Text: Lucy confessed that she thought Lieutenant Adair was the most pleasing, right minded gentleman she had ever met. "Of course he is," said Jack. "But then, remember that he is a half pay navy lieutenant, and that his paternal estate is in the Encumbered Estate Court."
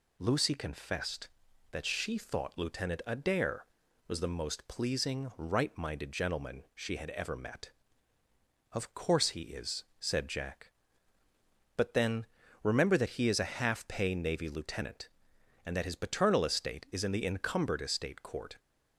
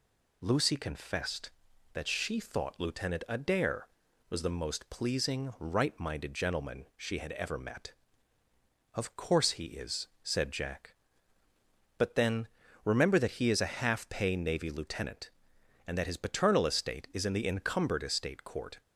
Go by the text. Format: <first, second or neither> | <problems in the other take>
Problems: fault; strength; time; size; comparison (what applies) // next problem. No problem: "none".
neither | none